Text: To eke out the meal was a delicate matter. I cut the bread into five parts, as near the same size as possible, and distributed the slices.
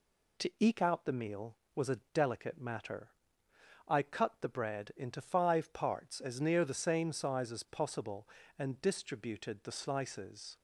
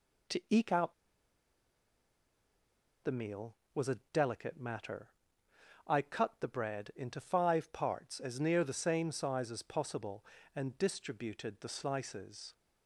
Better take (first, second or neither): first